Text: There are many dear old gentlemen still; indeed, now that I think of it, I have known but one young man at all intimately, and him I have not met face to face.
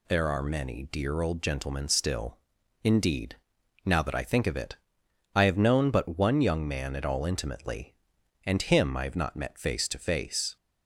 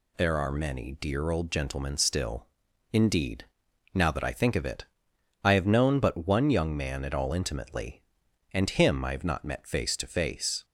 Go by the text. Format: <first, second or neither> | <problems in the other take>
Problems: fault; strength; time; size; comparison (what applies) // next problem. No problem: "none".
neither | none